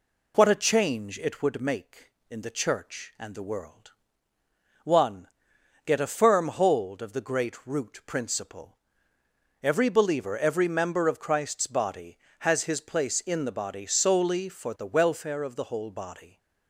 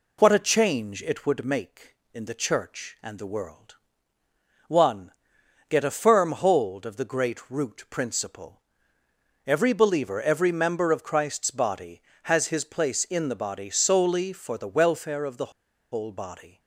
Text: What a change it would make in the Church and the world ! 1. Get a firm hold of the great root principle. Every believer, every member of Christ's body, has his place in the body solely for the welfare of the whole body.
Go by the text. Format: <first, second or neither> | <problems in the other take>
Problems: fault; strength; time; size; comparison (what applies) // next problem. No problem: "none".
first | pauses between "the" and "whole"; at 15.5 s; 0.42 s long